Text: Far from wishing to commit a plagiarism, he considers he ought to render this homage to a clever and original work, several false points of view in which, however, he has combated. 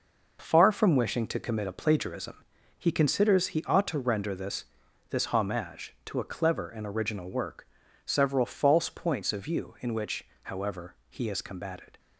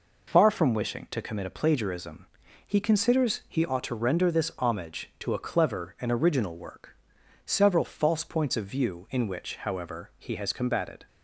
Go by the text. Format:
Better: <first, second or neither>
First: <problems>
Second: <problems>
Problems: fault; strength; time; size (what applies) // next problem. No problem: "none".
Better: second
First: says "this" twice; at 5.1 s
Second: none